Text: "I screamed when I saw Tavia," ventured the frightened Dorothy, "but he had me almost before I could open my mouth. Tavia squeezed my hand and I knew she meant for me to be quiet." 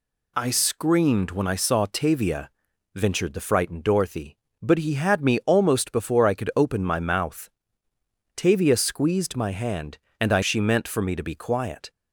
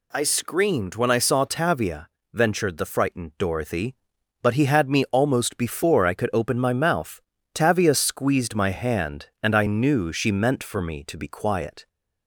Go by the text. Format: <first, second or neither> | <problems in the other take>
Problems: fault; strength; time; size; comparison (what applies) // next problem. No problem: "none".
second | skips "knew"; at 10.4 s